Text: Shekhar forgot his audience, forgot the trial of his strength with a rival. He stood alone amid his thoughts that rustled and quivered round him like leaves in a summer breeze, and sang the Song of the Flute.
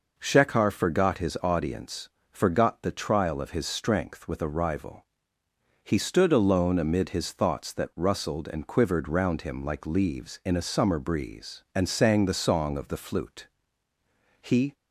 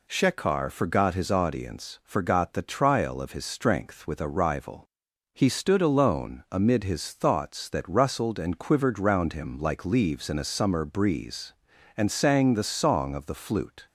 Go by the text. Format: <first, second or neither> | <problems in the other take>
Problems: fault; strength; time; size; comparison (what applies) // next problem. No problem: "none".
second | goes on to say "He"; slight; from 14.4 s on; 0.32 s long